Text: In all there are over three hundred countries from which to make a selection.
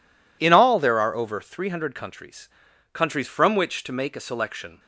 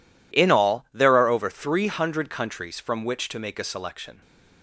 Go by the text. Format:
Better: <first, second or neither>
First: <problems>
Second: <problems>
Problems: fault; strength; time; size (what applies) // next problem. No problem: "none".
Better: second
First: says "countries" twice; at 2.9 s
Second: none